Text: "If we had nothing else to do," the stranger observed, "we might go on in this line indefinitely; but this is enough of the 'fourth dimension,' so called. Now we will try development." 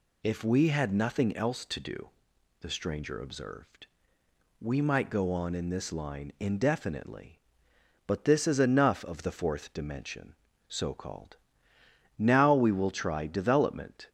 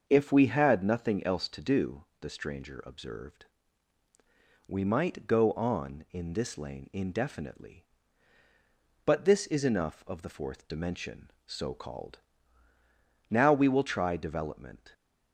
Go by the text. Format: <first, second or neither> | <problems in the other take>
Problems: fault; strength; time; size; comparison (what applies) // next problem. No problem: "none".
first | starts louder than the rest; until 1.0 s; 6.5 dB // says "lane" for "line"; at 6.5 s